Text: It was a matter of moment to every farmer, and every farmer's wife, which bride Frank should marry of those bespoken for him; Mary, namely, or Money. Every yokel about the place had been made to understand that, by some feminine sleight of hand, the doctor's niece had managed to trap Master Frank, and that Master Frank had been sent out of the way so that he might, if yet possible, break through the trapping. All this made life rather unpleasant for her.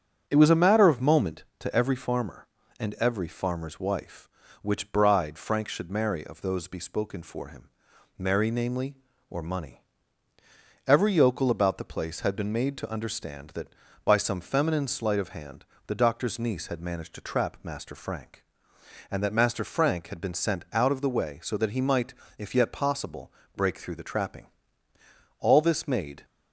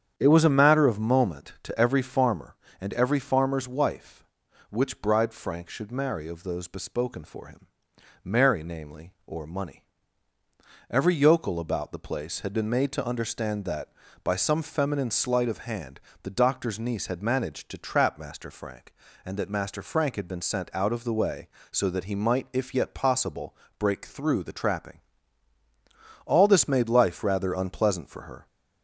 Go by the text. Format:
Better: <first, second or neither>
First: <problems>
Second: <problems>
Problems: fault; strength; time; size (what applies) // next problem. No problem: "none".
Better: second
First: starts louder than the rest; until 1.2 s; 7 dB // stops before "life rather unpleasant for her"; at 26.2 s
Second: starts louder than the rest; strong; until 1.1 s; 8.5 dB